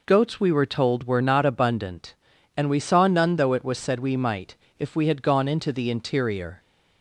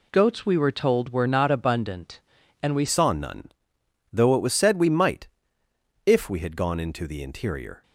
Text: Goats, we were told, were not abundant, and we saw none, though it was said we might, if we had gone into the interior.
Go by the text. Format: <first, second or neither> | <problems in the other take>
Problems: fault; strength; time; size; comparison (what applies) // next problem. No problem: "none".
first | changes voice at "saw"; from 2.8 s on; 5.0 s long